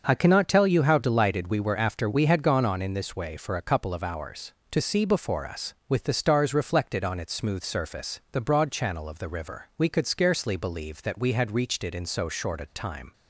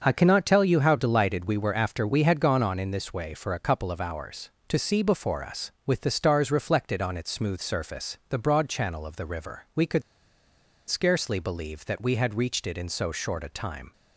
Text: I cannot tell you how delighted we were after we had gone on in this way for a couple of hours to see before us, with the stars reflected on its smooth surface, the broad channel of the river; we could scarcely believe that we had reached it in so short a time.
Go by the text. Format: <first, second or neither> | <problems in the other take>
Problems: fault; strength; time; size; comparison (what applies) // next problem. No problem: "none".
first | starts louder than the rest; until 1.0 s; 7 dB; also in the first // pauses between "could" and "scarcely"; noticeable; at 10.0 s; 0.85 s long